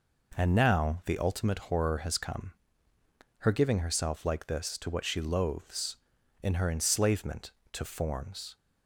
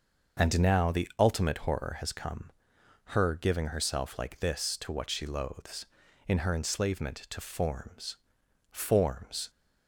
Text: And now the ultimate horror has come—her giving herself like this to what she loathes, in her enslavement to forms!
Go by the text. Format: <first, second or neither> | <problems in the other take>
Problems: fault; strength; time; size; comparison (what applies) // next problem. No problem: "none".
first | starts louder than the rest; until 1.4 s; 6.5 dB // says "forms" twice; at 8.6 s